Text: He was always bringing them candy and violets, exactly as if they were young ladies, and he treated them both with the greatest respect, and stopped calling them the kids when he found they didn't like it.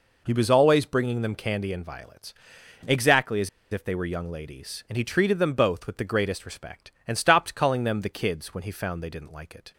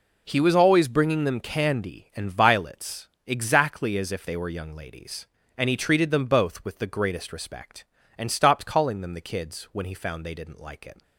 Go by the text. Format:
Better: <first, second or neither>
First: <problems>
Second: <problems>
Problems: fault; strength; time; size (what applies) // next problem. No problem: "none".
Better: second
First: pauses between "as" and "if"; slight; at 3.4 s; 0.23 s long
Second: none